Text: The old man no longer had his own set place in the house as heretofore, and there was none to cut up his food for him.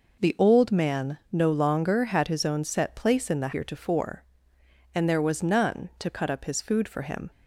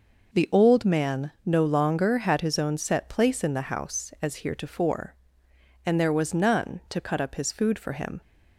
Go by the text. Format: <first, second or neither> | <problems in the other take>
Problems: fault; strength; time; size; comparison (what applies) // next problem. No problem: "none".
second | skips "house as"; at 3.5 s